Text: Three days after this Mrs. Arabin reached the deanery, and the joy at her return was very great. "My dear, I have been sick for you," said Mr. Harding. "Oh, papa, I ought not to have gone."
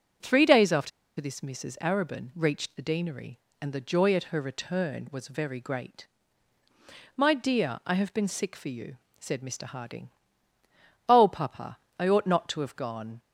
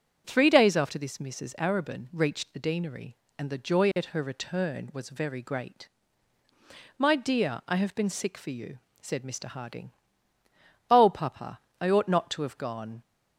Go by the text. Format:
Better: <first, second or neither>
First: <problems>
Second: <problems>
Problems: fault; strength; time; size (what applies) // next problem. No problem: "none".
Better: second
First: pauses between "after" and "this"; slight; at 0.9 s; 0.29 s long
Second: none